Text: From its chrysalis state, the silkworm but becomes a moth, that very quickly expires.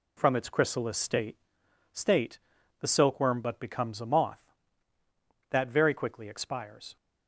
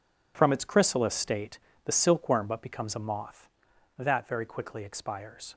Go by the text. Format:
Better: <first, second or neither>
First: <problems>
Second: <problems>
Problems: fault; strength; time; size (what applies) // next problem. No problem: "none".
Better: second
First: says "state" twice; at 1.9 s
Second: none